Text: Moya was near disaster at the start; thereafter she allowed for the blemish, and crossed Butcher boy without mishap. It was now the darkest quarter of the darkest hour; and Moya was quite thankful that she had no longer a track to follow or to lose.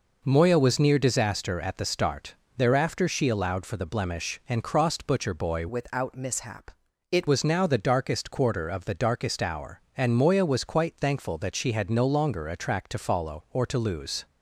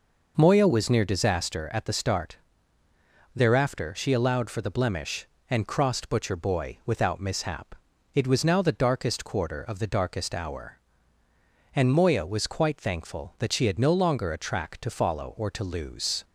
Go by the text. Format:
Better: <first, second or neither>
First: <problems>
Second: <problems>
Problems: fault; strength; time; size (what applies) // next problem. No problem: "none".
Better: second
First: changes voice from "without" to "It"; from 5.6 to 7.2 s; 1.6 s long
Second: none